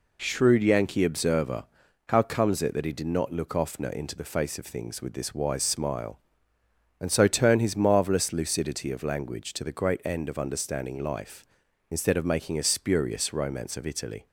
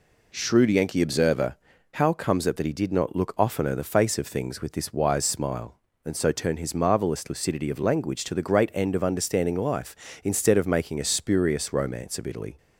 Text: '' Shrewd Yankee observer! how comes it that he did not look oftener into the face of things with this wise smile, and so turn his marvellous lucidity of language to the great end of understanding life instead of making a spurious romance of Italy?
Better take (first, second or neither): first